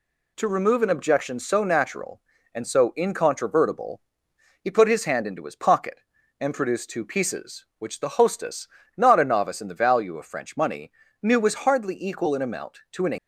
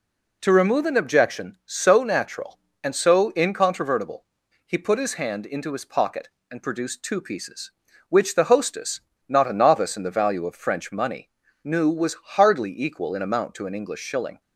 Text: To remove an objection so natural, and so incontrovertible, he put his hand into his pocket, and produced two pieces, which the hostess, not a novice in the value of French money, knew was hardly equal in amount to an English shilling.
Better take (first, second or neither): second